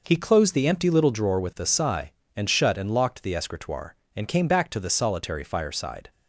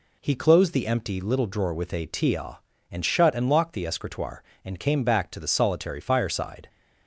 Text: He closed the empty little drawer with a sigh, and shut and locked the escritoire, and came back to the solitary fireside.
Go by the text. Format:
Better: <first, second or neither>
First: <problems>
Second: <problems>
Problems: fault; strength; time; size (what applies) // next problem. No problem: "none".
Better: first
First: none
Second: says "tia" for "sigh"; at 2.0 s